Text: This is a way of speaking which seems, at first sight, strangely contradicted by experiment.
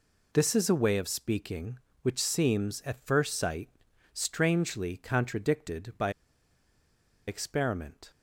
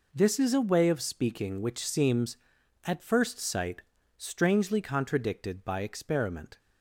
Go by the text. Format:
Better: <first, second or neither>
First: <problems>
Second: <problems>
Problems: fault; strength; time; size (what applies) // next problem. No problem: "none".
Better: second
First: pauses between "by" and "experiment"; at 6.1 s; 1.1 s long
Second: none